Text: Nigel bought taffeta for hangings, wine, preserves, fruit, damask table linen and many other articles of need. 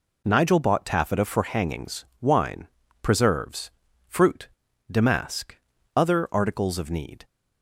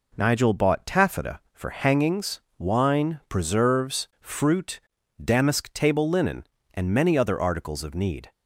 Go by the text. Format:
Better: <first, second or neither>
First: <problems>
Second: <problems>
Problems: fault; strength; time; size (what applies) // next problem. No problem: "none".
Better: second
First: skips "table linen and many"; at 5.7 s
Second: none